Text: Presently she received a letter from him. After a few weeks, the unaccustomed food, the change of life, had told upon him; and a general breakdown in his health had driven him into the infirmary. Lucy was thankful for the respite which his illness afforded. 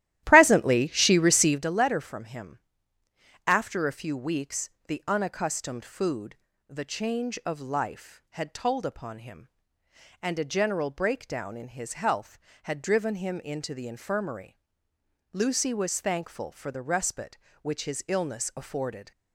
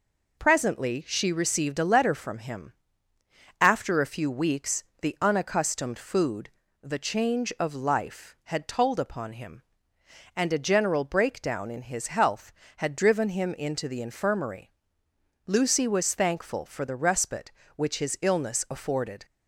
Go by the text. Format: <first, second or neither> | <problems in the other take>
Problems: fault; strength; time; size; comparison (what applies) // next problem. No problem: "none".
second | starts louder than the rest; strong; until 1.7 s; 14 dB